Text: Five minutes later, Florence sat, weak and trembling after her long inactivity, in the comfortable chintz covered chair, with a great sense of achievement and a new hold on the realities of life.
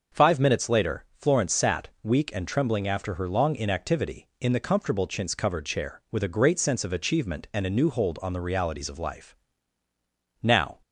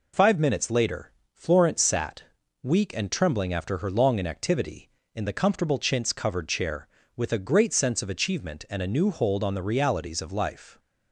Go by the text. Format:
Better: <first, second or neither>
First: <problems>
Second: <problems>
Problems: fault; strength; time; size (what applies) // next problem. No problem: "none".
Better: second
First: starts louder than the rest; noticeable; until 1.2 s; 6 dB // goes on to say "Now"; slight; from 10.4 s on; 0.38 s long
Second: none